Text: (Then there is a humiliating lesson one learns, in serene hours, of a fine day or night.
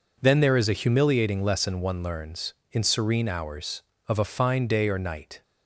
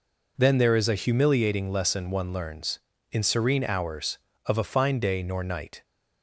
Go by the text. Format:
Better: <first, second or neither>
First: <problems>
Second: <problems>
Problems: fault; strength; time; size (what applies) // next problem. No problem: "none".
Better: first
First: none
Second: says "nor" for "or"; at 5.2 s